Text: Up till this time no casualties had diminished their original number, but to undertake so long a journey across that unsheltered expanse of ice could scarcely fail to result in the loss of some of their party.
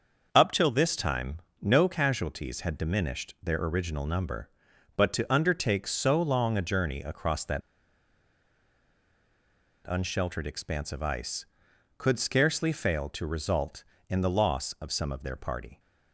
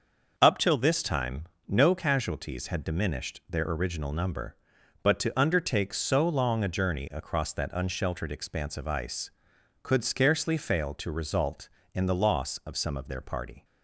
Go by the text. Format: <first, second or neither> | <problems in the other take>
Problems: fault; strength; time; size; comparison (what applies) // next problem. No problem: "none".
second | starts louder than the rest; until 1.3 s; 6 dB; also in the second // pauses between "time" and "no"; slight; at 1.3 s; 0.22 s long; slight in the second // pauses between "that" and "unsheltered"; strong; at 7.6 s; 2.2 s long